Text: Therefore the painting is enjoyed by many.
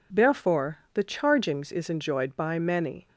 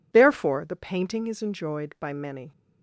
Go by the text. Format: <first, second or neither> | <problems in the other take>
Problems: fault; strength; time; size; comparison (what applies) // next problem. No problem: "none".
second | says "chargings" for "painting"; at 1.0 s